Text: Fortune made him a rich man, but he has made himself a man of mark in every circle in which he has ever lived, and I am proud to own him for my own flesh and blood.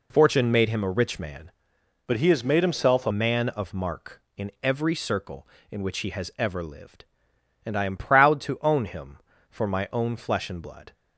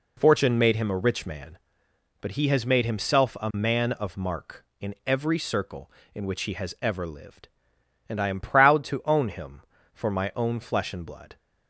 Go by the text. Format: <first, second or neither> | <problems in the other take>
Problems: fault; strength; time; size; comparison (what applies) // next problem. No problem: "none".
second | changes voice from "but" to "a"; from 2.0 to 3.1 s; 1.1 s long